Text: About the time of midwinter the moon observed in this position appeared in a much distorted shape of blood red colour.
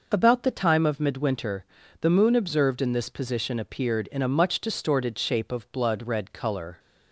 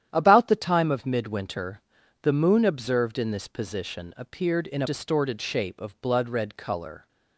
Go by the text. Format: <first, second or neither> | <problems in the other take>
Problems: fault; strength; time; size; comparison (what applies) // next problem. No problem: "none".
first | starts louder than the rest; strong; until 1.1 s; 10.5 dB // pauses between "midwinter" and "the"; at 1.8 s; 0.42 s long; slight in the first // skips "much"; at 4.8 s